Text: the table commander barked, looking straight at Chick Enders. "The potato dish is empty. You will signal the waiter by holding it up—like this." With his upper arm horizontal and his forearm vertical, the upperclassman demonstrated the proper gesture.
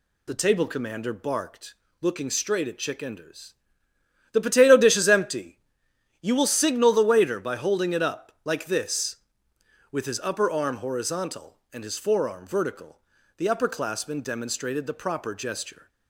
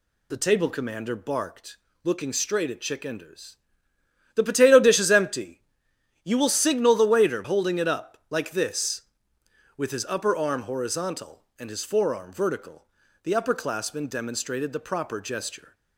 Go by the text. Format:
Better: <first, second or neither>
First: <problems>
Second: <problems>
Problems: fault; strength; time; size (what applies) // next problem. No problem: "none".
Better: first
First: none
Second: skips "by"; at 7.4 s